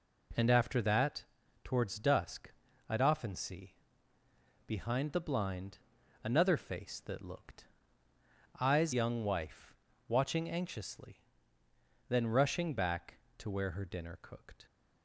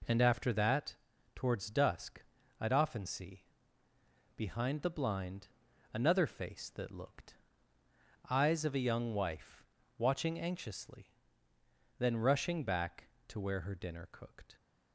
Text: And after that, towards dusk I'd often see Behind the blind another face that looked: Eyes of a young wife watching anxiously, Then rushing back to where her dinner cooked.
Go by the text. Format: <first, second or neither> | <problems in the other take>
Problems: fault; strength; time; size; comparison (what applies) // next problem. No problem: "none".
second | pauses between "dusk" and "I'd"; slight; at 2.5 s; 0.36 s long; slight in the second // pauses between "see" and "Behind"; noticeable; at 3.7 s; 0.92 s long; noticeable in the second // pauses between "blind" and "another"; noticeable; at 5.7 s; 0.46 s long; noticeable in the second // skips "of a"; at 8.9 s // pauses between "wife" and "watching"; slight; at 9.7 s; 0.36 s long; slight in the second